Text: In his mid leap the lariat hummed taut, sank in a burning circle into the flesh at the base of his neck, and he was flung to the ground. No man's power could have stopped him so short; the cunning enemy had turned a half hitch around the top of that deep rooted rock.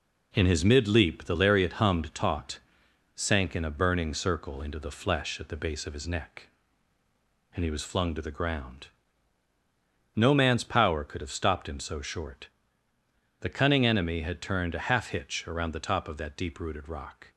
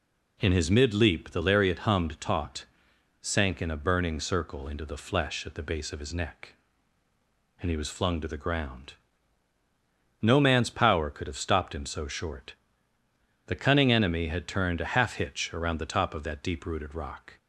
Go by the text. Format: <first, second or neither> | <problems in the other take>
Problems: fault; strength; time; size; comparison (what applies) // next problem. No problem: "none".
second | gets quieter; noticeable; throughout; 5 dB